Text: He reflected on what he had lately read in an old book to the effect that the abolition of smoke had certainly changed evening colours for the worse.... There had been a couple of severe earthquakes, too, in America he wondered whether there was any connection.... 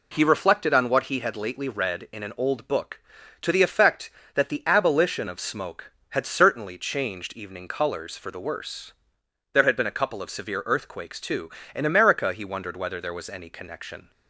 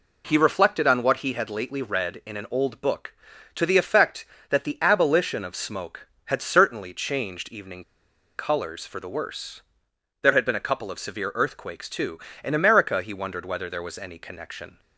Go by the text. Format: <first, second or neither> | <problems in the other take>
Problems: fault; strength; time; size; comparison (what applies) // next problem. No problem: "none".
first | pauses between "evening" and "colours"; noticeable; at 7.8 s; 0.53 s long